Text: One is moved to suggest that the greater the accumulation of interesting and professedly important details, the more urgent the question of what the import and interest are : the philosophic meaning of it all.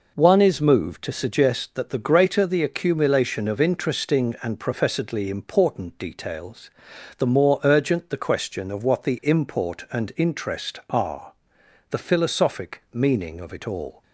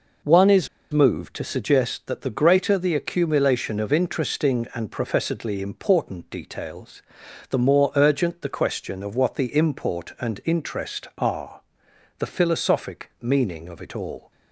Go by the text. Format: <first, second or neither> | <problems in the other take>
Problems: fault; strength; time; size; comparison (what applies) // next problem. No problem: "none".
first | pauses between "is" and "moved"; slight; at 0.6 s; 0.24 s long